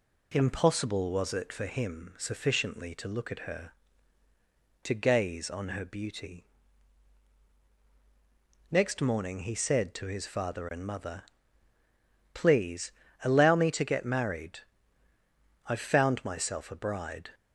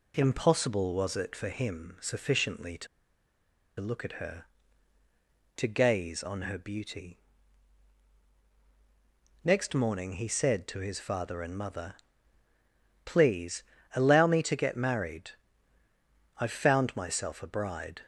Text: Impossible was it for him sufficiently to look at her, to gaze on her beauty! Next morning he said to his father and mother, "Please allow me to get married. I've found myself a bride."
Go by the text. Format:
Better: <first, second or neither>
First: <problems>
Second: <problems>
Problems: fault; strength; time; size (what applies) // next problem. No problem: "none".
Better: first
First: pauses between "Please" and "allow"; slight; at 12.9 s; 0.32 s long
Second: pauses between "to" and "look"; noticeable; at 2.8 s; 0.92 s long // pauses between "Please" and "allow"; slight; at 13.6 s; 0.32 s long